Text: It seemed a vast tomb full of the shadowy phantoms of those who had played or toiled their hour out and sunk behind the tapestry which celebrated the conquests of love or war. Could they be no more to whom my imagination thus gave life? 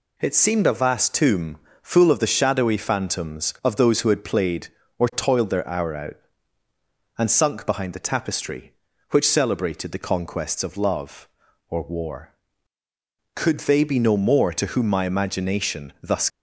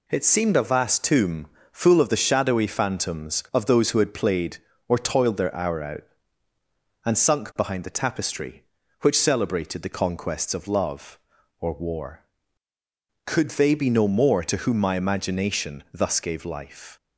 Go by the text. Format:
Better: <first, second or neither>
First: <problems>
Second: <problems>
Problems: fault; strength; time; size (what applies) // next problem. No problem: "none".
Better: second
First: pauses between "tomb" and "full"; slight; at 1.5 s; 0.26 s long // stops before "gave life"; at 16.2 s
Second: pauses between "tomb" and "full"; slight; at 1.4 s; 0.26 s long